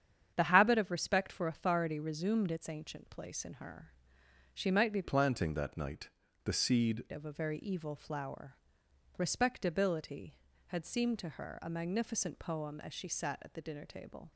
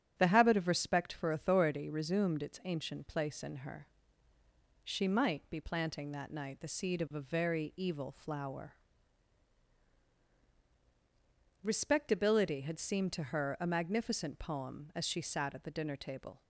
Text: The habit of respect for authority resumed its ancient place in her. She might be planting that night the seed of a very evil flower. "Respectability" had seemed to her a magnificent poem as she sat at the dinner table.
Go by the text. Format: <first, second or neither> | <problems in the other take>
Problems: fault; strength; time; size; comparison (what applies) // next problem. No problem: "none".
second | starts louder than the rest; strong; until 1.3 s; 8.5 dB; strong in the second // changes voice from "planting" to "seed"; from 5.0 to 7.0 s; 2.0 s long // pauses between "night" and "the"; slight; at 6.0 s; 0.34 s long